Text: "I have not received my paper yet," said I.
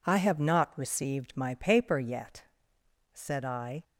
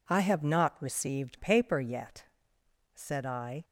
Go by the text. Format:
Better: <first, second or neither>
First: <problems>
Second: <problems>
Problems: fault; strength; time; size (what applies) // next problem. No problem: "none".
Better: first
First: none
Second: skips "my"; at 1.3 s